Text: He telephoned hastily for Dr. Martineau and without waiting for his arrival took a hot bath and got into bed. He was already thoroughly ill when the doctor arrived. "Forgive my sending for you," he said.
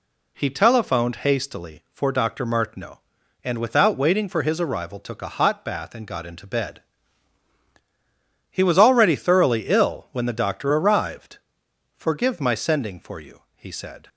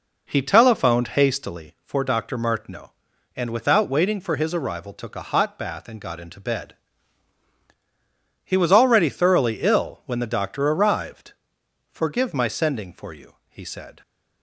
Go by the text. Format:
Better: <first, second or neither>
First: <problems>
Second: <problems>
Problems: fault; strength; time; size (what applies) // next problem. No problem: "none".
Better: first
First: none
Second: starts louder than the rest; noticeable; until 1.7 s; 4.5 dB